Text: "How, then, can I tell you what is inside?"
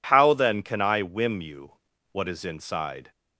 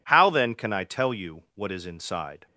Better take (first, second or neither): second